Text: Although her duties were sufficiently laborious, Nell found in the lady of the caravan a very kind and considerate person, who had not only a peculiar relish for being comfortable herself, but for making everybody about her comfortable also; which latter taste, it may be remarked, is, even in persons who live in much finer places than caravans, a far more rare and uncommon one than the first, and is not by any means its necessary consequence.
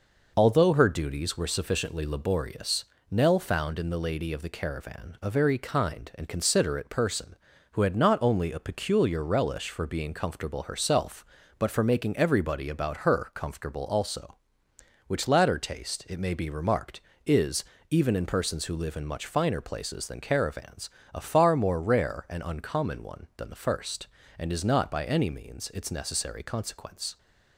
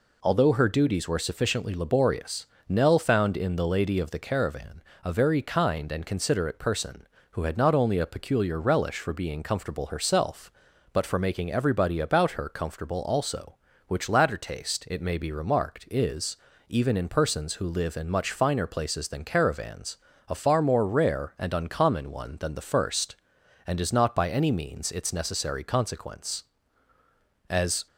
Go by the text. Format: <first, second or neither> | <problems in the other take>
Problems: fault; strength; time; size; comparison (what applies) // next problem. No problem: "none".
first | pauses between "caravan" and "a"; slight; at 4.8 s; 0.20 s long // goes on to say "As"; slight; from 27.4 s on; 0.38 s long